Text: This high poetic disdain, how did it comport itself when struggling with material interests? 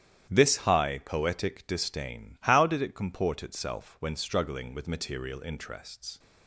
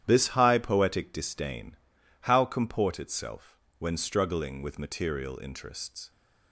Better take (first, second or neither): first